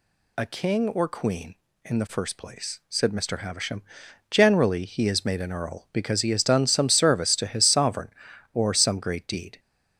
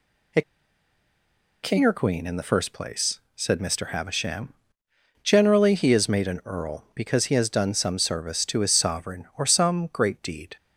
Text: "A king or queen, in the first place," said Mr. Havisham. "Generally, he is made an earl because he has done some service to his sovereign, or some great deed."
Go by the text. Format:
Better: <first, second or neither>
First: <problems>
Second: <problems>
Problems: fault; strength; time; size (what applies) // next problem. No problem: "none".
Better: first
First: none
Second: pauses between "A" and "king"; at 0.4 s; 1.2 s long